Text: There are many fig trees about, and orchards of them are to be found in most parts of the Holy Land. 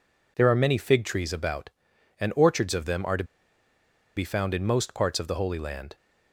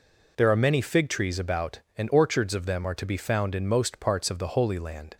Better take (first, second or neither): second